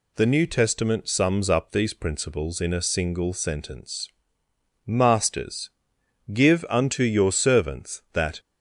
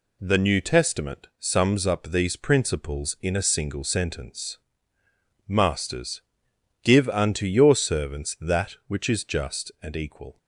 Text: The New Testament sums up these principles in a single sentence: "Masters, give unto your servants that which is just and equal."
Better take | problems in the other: second | stops before "which is just and equal"; at 8.3 s

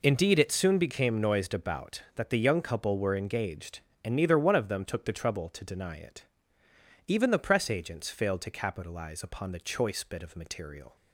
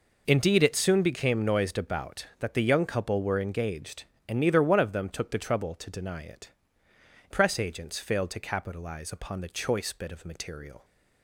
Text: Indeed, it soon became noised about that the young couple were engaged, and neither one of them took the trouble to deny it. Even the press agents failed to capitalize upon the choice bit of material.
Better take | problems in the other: first | skips "Even the"; at 6.8 s

